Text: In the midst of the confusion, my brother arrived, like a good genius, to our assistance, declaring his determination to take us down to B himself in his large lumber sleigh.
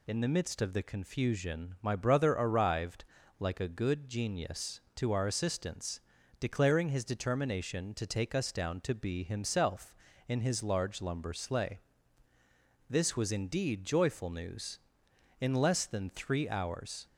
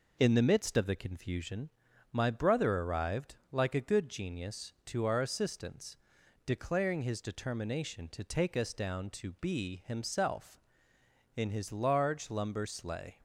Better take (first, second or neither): second